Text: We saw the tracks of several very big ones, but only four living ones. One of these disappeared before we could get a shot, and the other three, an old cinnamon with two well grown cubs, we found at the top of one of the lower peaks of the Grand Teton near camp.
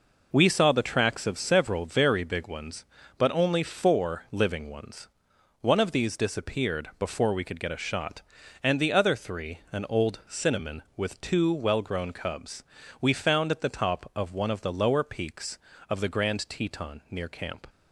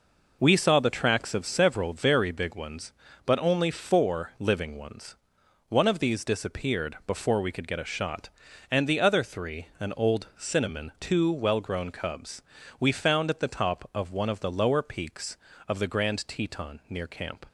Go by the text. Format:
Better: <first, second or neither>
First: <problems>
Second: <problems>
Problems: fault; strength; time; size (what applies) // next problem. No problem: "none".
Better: first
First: none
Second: skips "with"; at 10.9 s